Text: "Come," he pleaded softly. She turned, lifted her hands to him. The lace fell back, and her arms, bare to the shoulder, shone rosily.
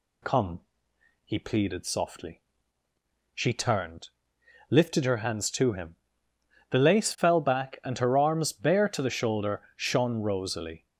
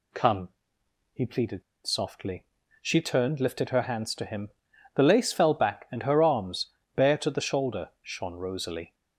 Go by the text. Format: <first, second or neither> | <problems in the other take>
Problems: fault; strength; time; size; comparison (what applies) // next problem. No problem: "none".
first | pauses between "pleaded" and "softly"; slight; at 1.6 s; 0.23 s long